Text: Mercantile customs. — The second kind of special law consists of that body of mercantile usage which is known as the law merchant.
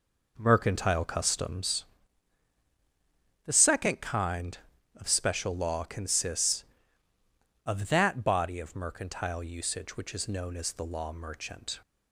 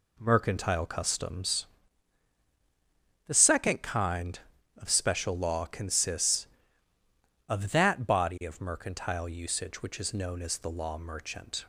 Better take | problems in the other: second | starts louder than the rest; noticeable; until 1.6 s; 5 dB

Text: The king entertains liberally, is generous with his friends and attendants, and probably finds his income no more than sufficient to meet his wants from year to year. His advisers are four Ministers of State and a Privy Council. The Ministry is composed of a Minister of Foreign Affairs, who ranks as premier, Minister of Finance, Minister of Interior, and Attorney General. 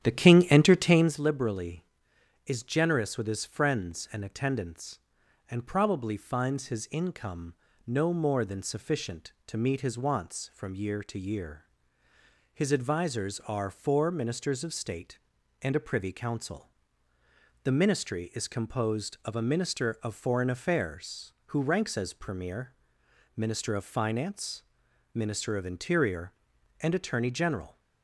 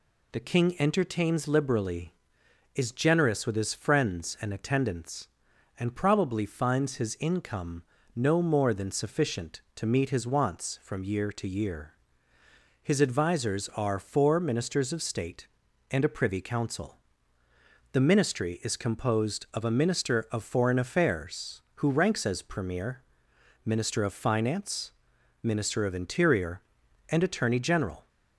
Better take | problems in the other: second | starts louder than the rest; strong; until 1.2 s; 10.5 dB // pauses between "income" and "no"; slight; at 7.5 s; 0.32 s long; slight in the second

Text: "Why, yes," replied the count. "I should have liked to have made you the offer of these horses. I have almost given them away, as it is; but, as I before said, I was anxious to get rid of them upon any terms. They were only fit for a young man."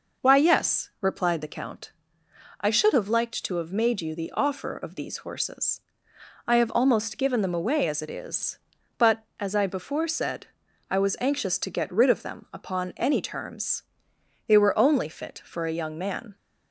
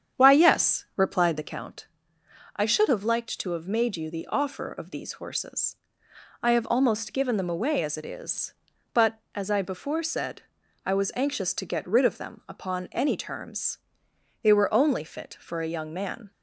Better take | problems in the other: first | starts louder than the rest; strong; until 1.6 s; 8.5 dB

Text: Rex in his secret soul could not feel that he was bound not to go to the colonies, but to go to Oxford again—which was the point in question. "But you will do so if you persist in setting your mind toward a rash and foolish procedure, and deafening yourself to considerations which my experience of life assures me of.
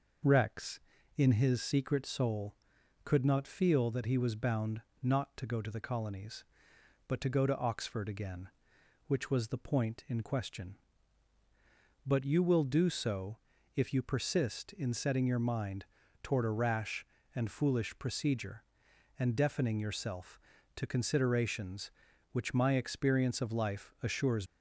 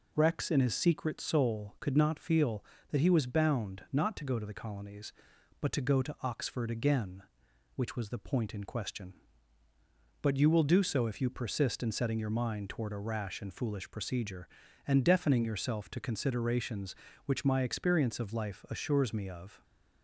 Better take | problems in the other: second | pauses between "bound" and "not"; slight; at 4.7 s; 0.22 s long // pauses between "so" and "if"; at 13.3 s; 0.40 s long // pauses between "mind" and "toward"; at 15.8 s; 0.38 s long // stops before "me of"; at 24.4 s

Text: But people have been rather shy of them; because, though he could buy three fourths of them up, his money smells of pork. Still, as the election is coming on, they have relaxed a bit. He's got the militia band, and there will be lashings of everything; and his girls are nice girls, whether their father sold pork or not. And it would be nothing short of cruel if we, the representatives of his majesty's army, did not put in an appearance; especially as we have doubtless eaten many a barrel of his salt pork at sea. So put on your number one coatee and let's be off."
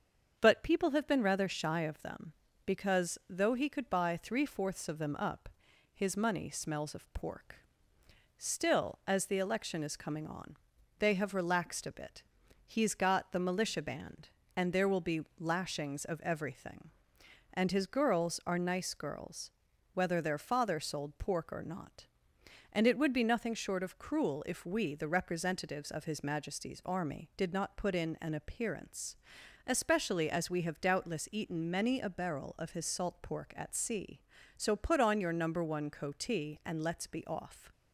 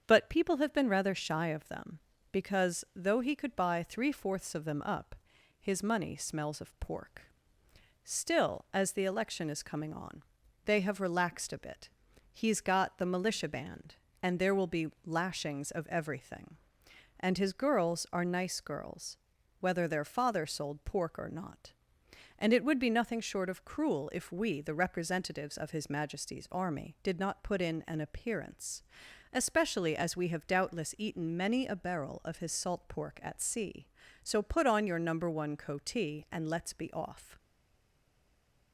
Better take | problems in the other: first | starts louder than the rest; until 1.0 s; 7 dB; also in the first // pauses between "be" and "lashings"; slight; at 14.8 s; 0.16 s long; slight in the first // stays silent after the last word; noticeable; from 37.3 s on; 1.4 s long

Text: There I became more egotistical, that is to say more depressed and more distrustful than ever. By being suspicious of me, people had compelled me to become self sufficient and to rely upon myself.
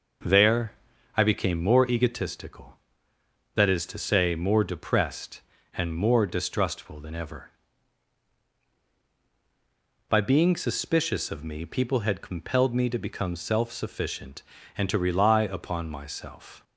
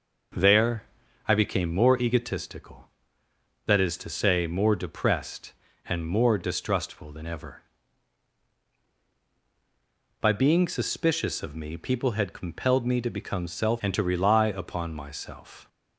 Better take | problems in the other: first | pauses between "There" and "I"; at 0.8 s; 0.42 s long; also in the first // skips "sufficient"; at 13.8 s

